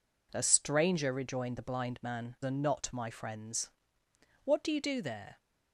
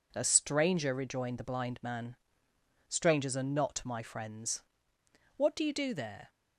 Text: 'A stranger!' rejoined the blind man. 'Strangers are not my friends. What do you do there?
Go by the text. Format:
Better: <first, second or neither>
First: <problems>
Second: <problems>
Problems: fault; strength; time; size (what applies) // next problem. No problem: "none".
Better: second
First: skips "Strangers"; at 2.3 s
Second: none